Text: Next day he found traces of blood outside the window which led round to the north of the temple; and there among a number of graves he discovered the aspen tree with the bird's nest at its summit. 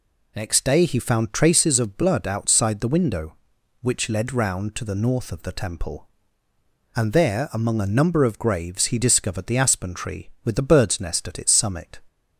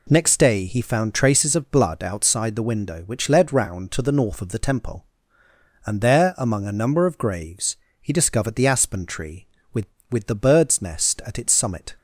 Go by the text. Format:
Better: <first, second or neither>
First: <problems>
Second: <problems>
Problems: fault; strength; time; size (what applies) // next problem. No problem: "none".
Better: first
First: none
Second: pauses between "graves" and "he"; slight; at 7.7 s; 0.24 s long // says "with" twice; at 10.0 s